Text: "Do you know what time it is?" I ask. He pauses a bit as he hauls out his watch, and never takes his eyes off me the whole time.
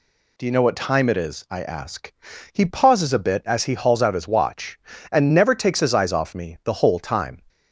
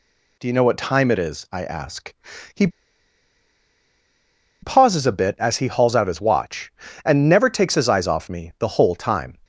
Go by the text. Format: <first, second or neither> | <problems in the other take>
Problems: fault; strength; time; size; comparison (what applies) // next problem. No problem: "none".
first | pauses between "He" and "pauses"; strong; at 2.6 s; 1.9 s long